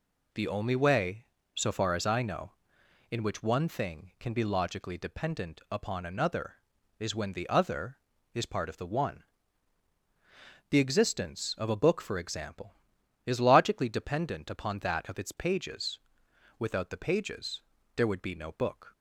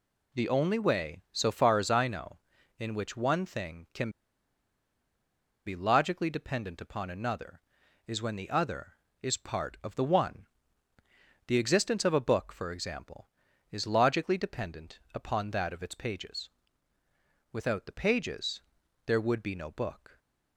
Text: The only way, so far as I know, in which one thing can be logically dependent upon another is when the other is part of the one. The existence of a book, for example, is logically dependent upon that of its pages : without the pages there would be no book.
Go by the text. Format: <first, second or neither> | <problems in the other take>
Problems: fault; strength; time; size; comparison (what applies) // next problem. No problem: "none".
first | pauses between "can" and "be"; strong; at 4.0 s; 1.5 s long // pauses between "pages" and "there"; at 18.6 s; 0.42 s long; slight in the first